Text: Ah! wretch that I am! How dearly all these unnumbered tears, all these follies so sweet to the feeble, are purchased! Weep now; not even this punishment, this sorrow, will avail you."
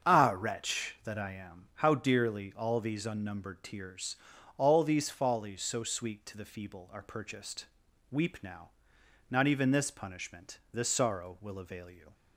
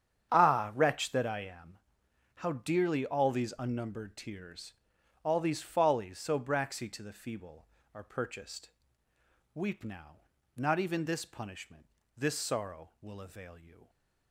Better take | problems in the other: first | starts louder than the rest; strong; until 1.3 s; 9 dB; strong in the first // says "braxy" for "sweet"; at 6.3 s

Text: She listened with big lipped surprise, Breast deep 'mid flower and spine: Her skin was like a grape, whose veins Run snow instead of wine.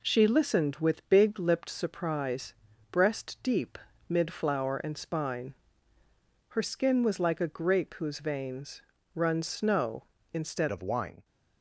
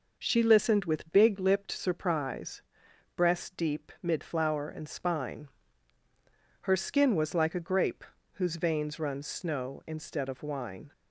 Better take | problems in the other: second | pauses between "deep" and "mid"; slight; at 3.7 s; 0.30 s long // pauses between "veins" and "Run"; slight; at 8.8 s; 0.34 s long // changes voice at "of"; from 10.7 s on; 0.5 s long

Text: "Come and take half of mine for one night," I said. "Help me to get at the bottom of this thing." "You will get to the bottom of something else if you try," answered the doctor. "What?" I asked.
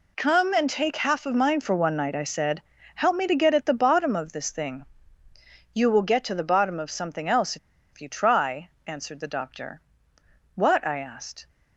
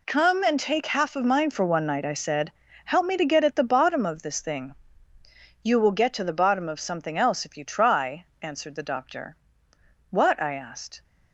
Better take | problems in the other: second | pauses between "else" and "if"; at 7.5 s; 0.36 s long

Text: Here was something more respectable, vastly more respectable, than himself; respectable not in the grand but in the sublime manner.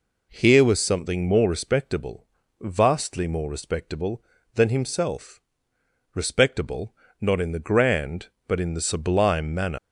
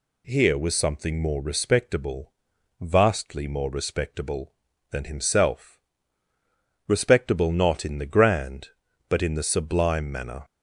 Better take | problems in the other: second | pauses between "respectable" and "not"; slight; at 6.9 s; 0.26 s long // leaves "manner" unfinished; at 9.7 s; 100 ms

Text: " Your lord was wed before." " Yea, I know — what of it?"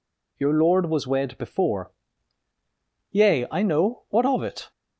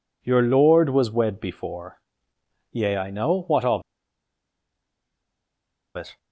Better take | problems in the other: first | pauses between "of" and "it"; strong; at 3.8 s; 2.1 s long

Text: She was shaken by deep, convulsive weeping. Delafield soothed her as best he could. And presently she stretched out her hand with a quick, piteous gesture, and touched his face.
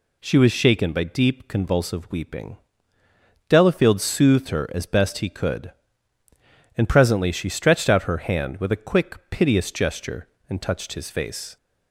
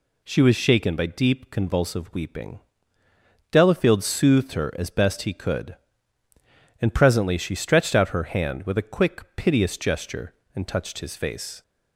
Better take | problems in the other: neither | none

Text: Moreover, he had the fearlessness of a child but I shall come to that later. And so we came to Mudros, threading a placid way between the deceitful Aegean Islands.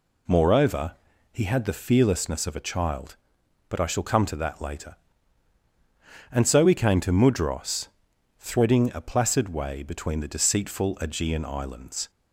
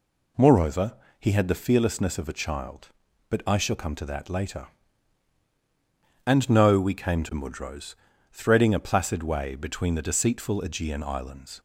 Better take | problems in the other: first | says "no" for "so"; at 6.4 s

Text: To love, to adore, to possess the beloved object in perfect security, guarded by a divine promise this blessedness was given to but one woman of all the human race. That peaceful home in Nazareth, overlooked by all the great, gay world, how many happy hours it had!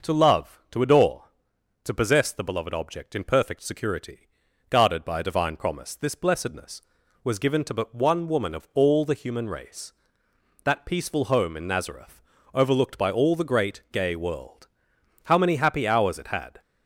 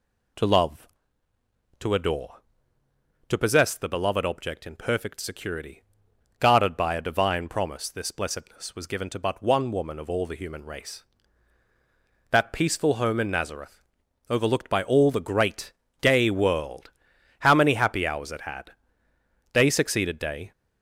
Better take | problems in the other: first | goes on to say "Day succeeded day"; noticeable; from 19.5 s on; 0.98 s long

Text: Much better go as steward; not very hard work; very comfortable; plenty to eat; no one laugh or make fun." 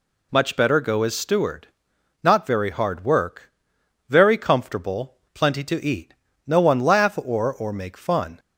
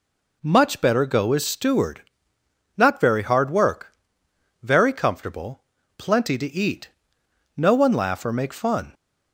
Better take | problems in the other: second | says "or" twice; at 7.5 s

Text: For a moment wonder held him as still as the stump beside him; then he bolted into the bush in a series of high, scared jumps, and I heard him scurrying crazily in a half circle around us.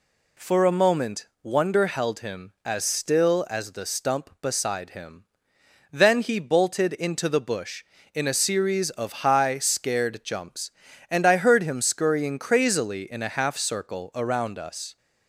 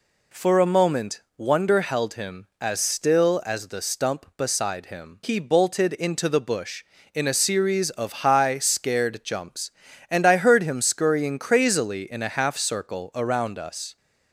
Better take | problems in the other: first | pauses between "moment" and "wonder"; slight; at 1.2 s; 0.16 s long; slight in the first // skips "then"; at 5.2 s

